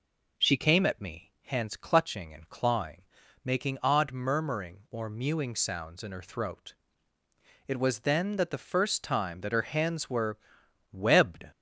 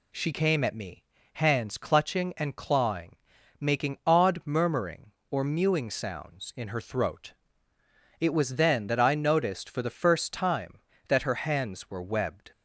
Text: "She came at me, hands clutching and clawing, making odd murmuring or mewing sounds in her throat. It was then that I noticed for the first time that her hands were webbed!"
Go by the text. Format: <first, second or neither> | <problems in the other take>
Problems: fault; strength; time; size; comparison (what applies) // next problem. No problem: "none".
second | skips "I noticed for"; at 8.4 s // pauses between "were" and "webbed"; noticeable; at 10.3 s; 0.54 s long